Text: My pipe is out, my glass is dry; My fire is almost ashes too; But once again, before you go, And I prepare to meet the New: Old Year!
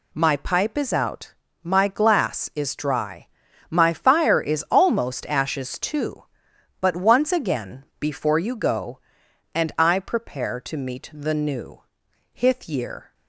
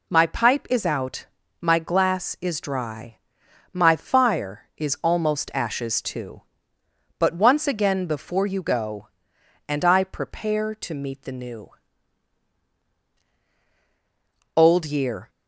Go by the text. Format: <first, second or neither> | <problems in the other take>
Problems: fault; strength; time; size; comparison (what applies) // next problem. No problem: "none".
second | says "Hith" for "Old"; at 12.3 s